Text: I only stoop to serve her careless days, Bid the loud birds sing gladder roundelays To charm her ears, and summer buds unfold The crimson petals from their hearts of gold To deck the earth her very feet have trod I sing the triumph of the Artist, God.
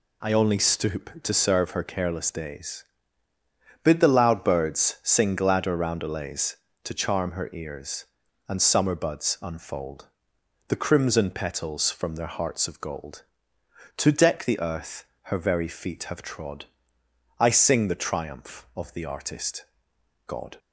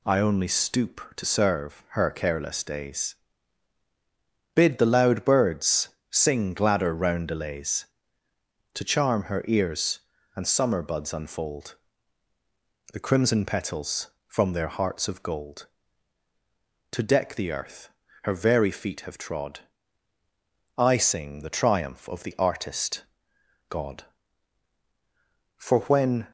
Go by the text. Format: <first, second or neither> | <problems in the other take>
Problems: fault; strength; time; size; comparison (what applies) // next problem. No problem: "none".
first | pauses between "birds" and "sing"; slight; at 5.8 s; 0.20 s long // pauses between "unfold" and "The"; at 11.7 s; 1.1 s long; noticeable in the first // pauses between "earth" and "her"; slight; at 17.8 s; 0.34 s long; slight in the first // pauses between "trod" and "I"; at 19.5 s; 1.1 s long; noticeable in the first // goes on to say "For when"; noticeable; from 25.5 s on; 0.68 s long